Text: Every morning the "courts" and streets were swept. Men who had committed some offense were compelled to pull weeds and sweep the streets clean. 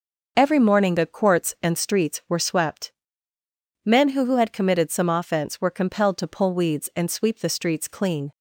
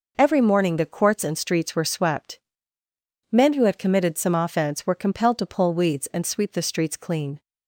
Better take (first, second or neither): second